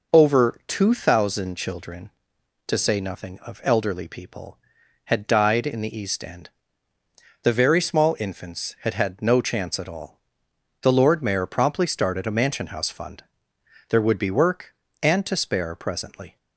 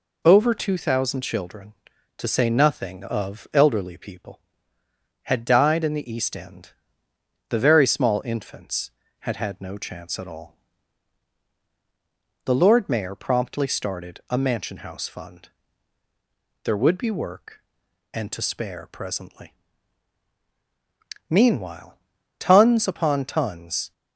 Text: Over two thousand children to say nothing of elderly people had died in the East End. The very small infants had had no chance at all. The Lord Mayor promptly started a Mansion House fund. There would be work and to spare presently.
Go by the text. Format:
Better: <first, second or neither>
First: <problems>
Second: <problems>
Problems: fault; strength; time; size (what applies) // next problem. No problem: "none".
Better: first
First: none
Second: goes on to say "Meanwhile tons upon tons"; strong; from 21.3 s on; 2.6 s long